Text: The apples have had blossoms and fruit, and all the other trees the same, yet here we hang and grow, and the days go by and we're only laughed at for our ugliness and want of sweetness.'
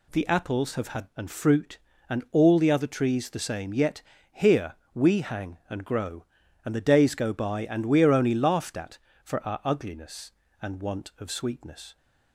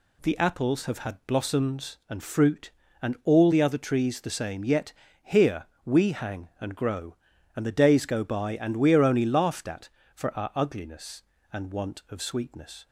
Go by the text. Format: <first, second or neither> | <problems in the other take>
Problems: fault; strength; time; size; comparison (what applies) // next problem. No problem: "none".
second | skips "blossoms"; at 1.1 s // pauses between "yet" and "here"; slight; at 4.0 s; 0.30 s long; slight in the second // pauses between "here" and "we"; slight; at 4.7 s; 0.20 s long; slight in the second